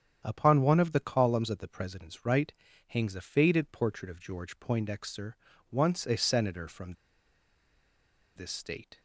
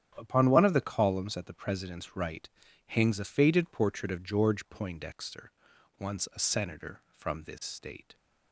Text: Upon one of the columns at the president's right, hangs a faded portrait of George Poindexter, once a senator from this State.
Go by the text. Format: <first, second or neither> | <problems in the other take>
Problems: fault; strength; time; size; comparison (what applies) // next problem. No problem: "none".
second | starts louder than the rest; strong; until 1.2 s; 9 dB; strong in the second // pauses between "from" and "this"; strong; at 6.9 s; 1.4 s long